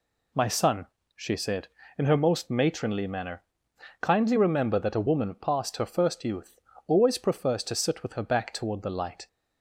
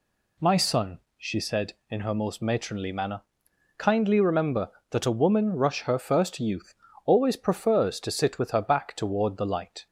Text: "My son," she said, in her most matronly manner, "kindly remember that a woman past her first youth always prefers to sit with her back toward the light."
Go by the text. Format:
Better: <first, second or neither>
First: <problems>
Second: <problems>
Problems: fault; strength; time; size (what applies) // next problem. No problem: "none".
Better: first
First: pauses between "youth" and "always"; slight; at 6.5 s; 0.32 s long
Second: says "rush" for "past"; at 5.5 s // pauses between "youth" and "always"; slight; at 6.7 s; 0.30 s long